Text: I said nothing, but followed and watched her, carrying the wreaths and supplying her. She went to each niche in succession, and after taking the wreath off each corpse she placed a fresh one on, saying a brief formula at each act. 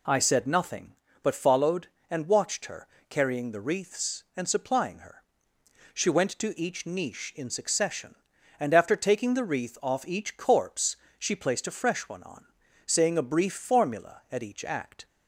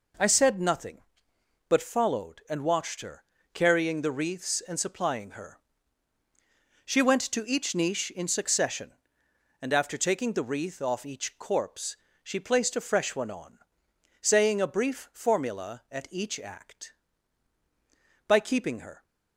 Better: first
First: pauses between "corpse" and "she"; slight; at 10.9 s; 0.22 s long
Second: pauses between "corpse" and "she"; slight; at 11.9 s; 0.26 s long // goes on to say "By keeping her"; noticeable; from 18.2 s on; 0.76 s long

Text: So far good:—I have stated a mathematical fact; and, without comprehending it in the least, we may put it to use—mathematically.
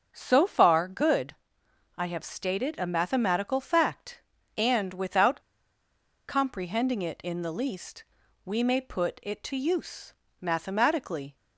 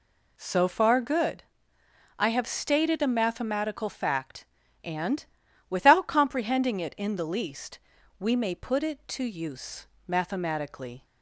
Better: second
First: starts louder than the rest; until 1.1 s; 6.5 dB // pauses between "without" and "comprehending"; noticeable; at 5.3 s; 0.89 s long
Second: none

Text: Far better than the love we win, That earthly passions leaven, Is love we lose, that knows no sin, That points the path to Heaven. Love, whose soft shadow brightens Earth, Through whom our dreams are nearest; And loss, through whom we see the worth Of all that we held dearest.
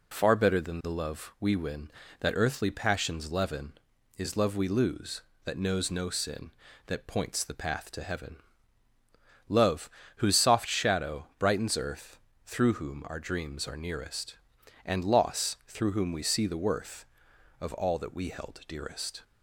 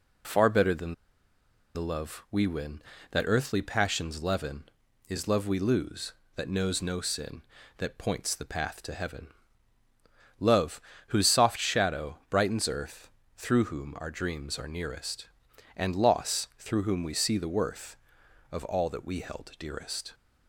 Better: first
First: none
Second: pauses between "than" and "the"; noticeable; at 0.9 s; 0.81 s long

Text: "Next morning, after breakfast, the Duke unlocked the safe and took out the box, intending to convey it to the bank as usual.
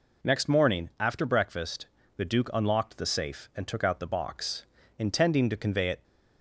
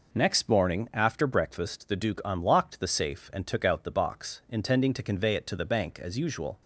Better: second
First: stops before "to the bank as usual"; at 6.0 s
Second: none

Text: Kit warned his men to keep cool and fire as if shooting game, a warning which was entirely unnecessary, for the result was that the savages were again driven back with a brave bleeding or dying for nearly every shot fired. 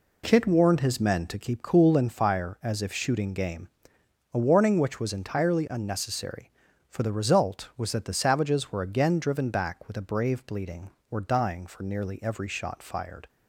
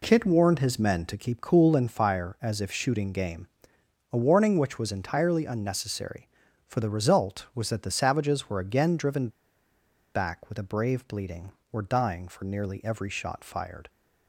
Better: first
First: none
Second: pauses between "driven" and "back"; noticeable; at 9.2 s; 0.85 s long

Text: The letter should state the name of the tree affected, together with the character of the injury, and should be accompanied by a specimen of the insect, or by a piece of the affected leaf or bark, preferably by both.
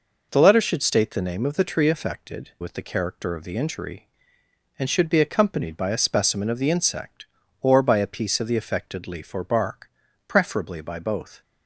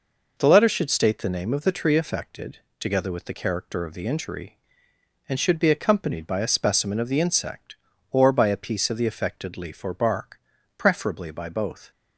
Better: second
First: skips "together"; at 2.5 s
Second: none

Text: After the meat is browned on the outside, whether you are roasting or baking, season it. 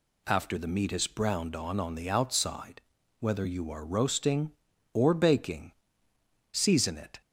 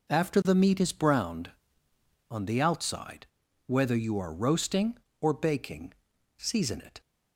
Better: second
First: says "on" twice; at 1.7 s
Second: none

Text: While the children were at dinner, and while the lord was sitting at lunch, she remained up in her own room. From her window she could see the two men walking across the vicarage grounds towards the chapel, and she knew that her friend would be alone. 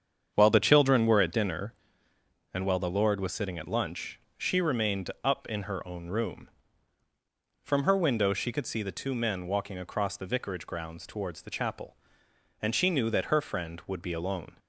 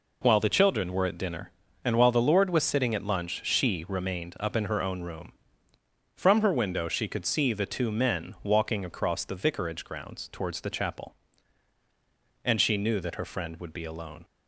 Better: second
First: starts louder than the rest; strong; until 1.5 s; 7.5 dB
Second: none

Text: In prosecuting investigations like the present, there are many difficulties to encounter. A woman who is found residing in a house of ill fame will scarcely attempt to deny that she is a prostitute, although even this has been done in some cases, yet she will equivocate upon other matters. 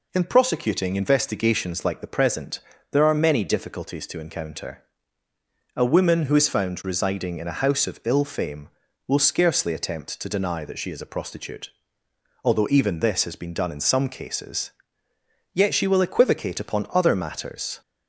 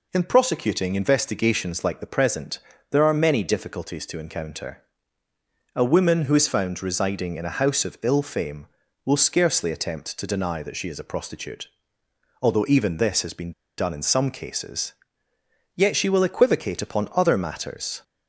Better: first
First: none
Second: pauses between "been" and "done"; slight; at 13.5 s; 0.27 s long

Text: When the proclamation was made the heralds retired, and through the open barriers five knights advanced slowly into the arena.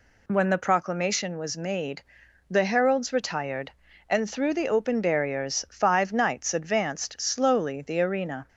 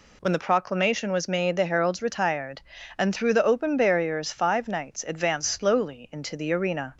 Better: second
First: pauses between "made" and "the"; noticeable; at 2.0 s; 0.48 s long // skips "into"; at 7.8 s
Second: none

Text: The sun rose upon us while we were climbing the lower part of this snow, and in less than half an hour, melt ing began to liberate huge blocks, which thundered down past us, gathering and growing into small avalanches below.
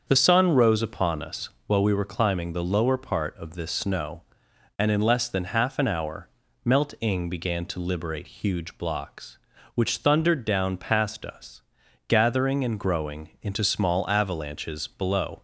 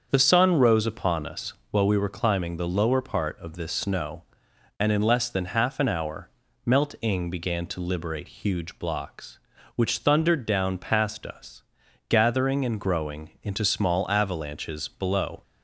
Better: neither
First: starts louder than the rest; until 1.0 s; 7 dB // pauses between "us" and "while"; slight; at 1.4 s; 0.16 s long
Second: starts louder than the rest; until 1.1 s; 7 dB // pauses between "us" and "while"; slight; at 1.5 s; 0.16 s long

